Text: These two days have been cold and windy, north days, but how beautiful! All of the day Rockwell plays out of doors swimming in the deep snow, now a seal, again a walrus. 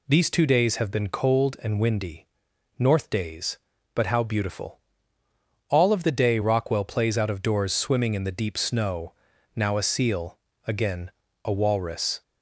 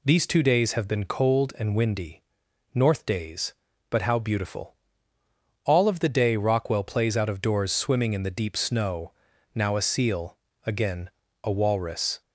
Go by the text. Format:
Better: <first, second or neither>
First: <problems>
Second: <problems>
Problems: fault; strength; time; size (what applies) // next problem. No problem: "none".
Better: neither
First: pauses between "again" and "a"; slight; at 11.1 s; 0.32 s long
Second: pauses between "again" and "a"; slight; at 11.1 s; 0.32 s long